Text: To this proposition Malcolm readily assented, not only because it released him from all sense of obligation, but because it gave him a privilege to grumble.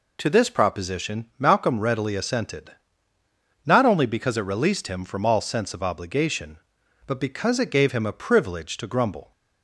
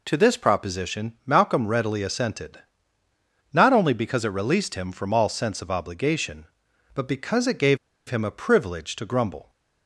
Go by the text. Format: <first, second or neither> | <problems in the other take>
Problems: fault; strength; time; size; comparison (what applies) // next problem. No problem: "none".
first | pauses between "gave" and "him"; slight; at 7.7 s; 0.31 s long